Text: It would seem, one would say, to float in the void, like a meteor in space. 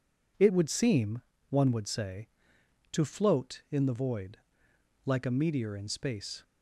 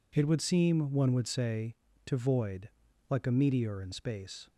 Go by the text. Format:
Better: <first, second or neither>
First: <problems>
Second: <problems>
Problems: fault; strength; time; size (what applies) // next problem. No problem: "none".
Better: first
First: none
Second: skips "float in the"; at 2.1 s